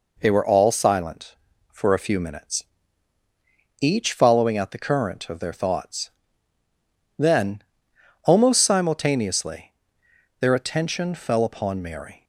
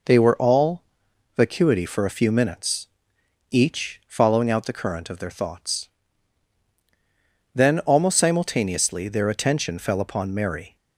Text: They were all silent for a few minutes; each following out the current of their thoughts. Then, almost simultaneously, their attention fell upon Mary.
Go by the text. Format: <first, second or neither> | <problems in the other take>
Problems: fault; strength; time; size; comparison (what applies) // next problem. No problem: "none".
first | says "vacuity" for "silent"; at 1.3 s